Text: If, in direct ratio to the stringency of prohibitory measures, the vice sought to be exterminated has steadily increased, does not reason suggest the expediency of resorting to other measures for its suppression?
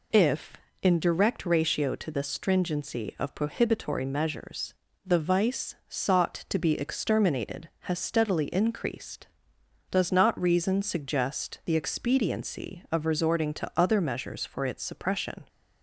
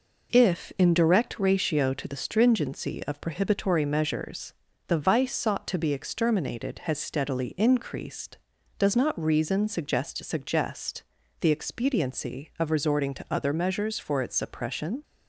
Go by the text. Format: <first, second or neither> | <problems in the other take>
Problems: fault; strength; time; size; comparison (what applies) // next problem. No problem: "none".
first | says "suggest" twice; at 10.2 s